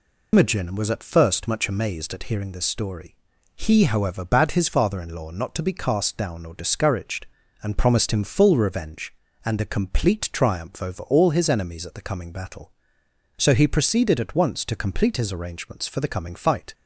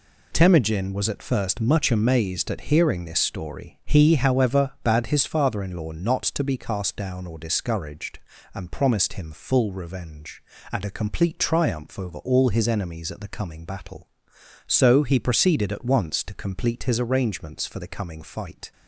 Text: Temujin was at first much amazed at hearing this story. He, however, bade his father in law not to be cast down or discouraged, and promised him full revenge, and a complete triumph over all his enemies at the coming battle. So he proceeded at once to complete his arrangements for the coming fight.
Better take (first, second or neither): second